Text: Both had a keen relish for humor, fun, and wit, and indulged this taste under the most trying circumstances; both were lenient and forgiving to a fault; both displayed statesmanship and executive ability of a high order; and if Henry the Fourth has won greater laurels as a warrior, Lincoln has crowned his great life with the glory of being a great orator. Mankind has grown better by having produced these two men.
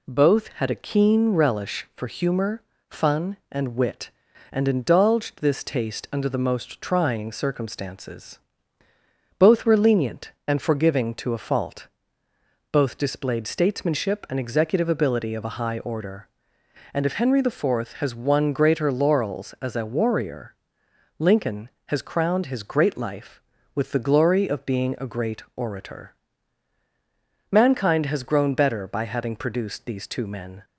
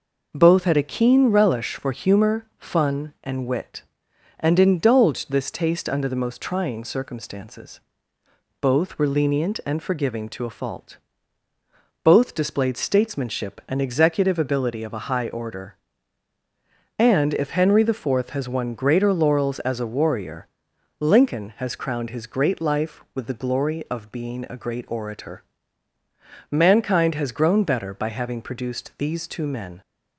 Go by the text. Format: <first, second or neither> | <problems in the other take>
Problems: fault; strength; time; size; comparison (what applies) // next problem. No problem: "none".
neither | none